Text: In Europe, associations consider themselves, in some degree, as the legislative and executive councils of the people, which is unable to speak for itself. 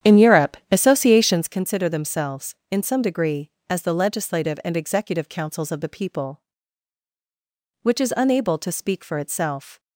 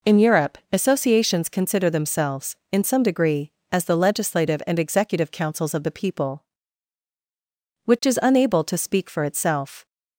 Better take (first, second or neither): second